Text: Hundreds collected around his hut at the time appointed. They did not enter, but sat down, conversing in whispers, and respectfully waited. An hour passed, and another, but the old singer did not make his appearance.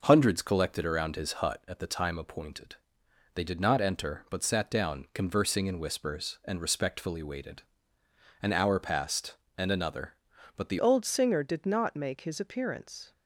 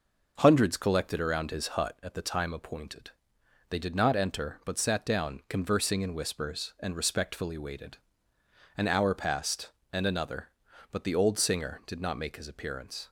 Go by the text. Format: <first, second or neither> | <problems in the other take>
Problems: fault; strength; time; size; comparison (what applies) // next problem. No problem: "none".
second | changes voice at "old"; from 10.7 s on; 2.4 s long